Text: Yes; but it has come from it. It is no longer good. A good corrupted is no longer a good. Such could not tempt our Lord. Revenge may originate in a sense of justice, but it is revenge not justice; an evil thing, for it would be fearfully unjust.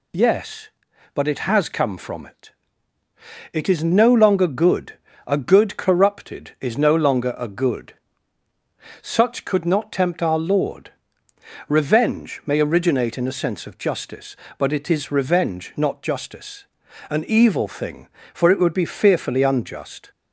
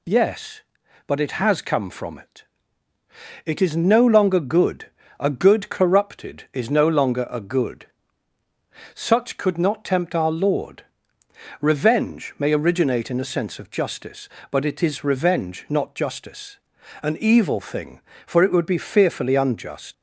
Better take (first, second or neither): first